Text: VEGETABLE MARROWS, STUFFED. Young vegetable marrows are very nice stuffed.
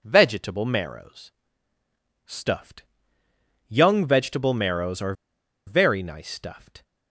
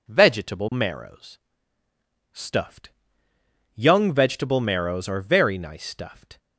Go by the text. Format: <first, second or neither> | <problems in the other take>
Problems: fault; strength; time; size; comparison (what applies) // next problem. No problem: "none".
second | pauses between "are" and "very"; noticeable; at 5.1 s; 0.53 s long